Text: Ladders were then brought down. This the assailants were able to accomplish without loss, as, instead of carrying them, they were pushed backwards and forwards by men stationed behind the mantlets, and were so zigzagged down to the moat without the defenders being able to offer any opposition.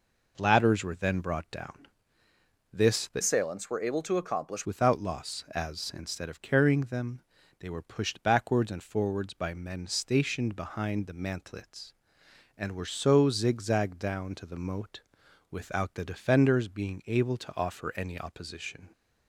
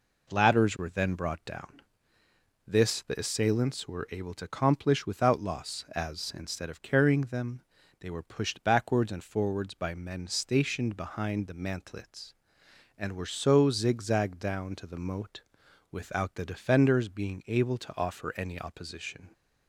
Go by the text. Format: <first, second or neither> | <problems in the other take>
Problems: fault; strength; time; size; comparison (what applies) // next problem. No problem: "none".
second | changes voice from "assailants" to "accomplish"; from 3.2 to 4.6 s; 1.4 s long // pauses between "moat" and "without"; noticeable; at 15.0 s; 0.50 s long; noticeable in the second